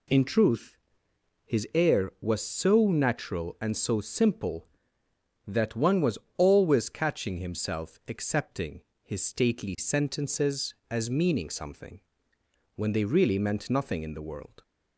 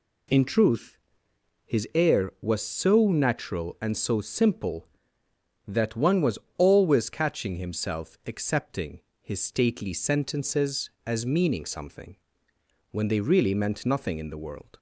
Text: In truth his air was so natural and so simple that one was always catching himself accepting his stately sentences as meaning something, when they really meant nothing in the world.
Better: neither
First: pauses between "truth" and "his"; noticeable; at 0.7 s; 0.70 s long // pauses between "was" and "always"; slight; at 6.1 s; 0.20 s long // pauses between "accepting" and "his"; slight; at 8.8 s; 0.22 s long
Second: pauses between "truth" and "his"; noticeable; at 0.9 s; 0.70 s long // pauses between "was" and "always"; slight; at 6.3 s; 0.20 s long // pauses between "accepting" and "his"; slight; at 8.9 s; 0.22 s long

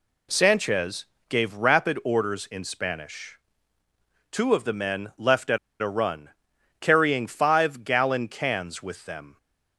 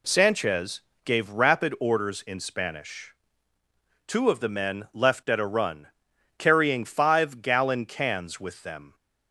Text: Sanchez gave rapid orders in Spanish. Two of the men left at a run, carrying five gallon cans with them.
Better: second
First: pauses between "Sanchez" and "gave"; slight; at 1.0 s; 0.22 s long // pauses between "at" and "a"; slight; at 5.5 s; 0.22 s long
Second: pauses between "Sanchez" and "gave"; slight; at 0.8 s; 0.22 s long

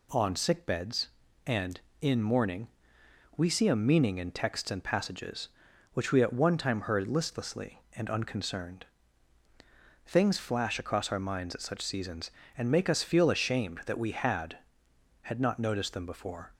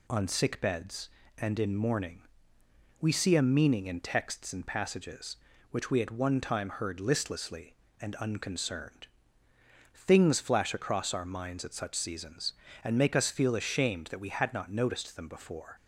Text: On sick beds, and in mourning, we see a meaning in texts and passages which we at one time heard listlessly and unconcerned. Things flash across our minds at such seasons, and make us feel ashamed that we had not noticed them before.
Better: second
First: says "had" twice; at 15.2 s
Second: none

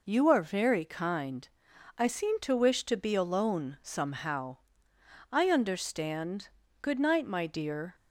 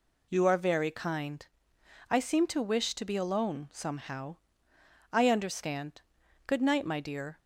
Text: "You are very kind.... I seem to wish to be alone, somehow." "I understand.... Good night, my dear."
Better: neither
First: none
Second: none

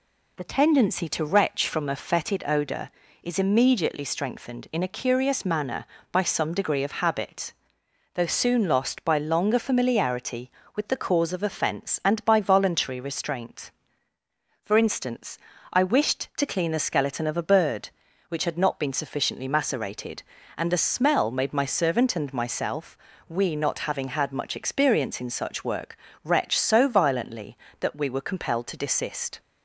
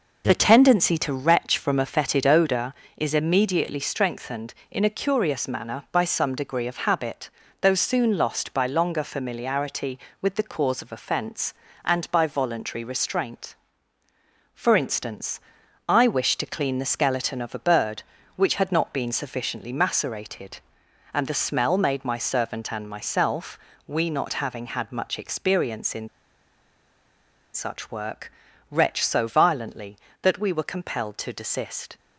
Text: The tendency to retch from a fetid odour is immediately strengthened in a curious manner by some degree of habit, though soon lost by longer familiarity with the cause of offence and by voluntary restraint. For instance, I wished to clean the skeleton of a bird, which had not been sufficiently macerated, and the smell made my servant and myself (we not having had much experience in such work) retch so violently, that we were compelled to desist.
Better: first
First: none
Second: pauses between "in" and "such"; strong; at 26.0 s; 1.4 s long

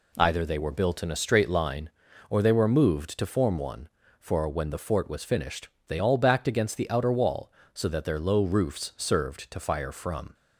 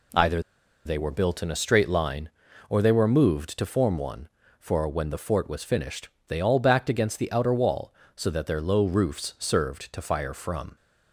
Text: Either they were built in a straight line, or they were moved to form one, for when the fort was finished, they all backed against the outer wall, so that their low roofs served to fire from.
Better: first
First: none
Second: pauses between "Either" and "they"; at 0.4 s; 0.44 s long

